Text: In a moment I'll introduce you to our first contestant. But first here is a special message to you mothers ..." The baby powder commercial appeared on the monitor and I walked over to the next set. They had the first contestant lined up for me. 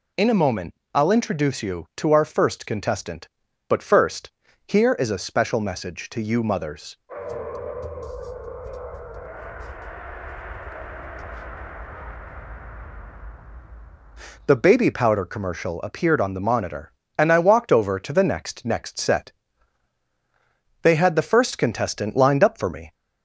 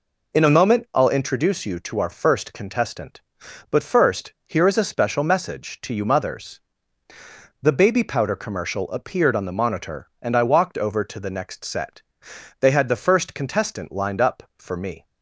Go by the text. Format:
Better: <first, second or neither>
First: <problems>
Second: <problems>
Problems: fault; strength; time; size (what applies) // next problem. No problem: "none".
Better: second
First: pauses between "moment" and "I'll"; slight; at 0.7 s; 0.18 s long // pauses between "first" and "here"; at 4.2 s; 0.38 s long // says "next" twice; at 18.6 s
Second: none